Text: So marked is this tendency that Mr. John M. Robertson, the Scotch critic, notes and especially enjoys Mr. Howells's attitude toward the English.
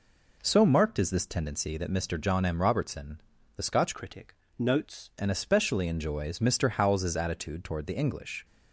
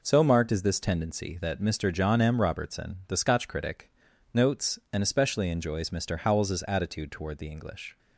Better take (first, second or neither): second